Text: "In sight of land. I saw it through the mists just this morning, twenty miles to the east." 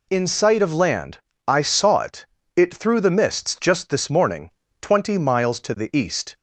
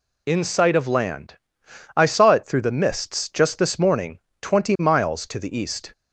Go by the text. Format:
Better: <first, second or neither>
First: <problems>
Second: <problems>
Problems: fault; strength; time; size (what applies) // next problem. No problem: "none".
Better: second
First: says "it" twice; at 2.5 s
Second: none